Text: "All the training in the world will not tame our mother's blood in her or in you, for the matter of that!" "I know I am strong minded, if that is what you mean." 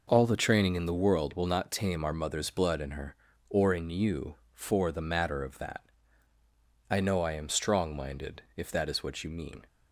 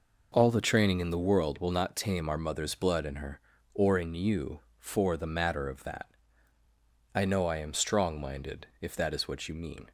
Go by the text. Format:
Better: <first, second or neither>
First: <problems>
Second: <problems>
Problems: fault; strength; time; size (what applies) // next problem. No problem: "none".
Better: neither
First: none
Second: none